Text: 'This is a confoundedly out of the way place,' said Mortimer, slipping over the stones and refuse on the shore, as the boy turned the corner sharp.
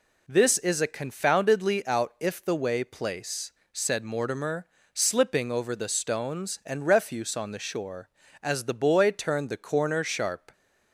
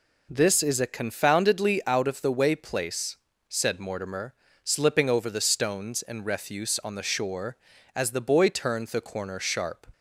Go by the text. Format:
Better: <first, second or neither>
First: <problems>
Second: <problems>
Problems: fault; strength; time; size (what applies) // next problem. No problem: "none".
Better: second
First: says "if" for "of"; at 2.2 s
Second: none